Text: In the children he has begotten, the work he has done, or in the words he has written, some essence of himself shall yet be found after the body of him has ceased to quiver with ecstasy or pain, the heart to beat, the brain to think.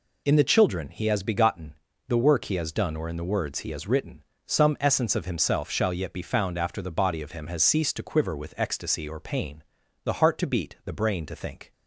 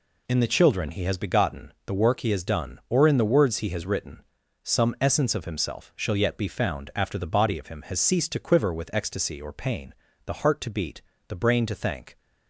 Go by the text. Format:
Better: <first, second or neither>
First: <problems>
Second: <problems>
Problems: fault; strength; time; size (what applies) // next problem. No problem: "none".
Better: first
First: none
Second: says "thank" for "think"; at 11.7 s